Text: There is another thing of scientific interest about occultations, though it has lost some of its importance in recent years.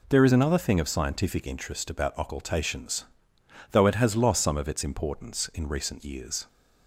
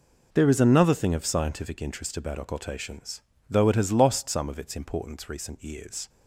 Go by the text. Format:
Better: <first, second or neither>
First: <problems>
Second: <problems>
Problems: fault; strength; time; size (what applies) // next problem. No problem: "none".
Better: first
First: none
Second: skips "in"; at 5.2 s